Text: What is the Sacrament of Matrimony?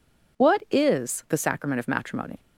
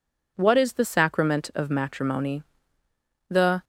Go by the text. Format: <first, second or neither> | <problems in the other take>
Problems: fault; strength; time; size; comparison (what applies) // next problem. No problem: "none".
first | goes on to say "The"; slight; from 3.2 s on; 0.34 s long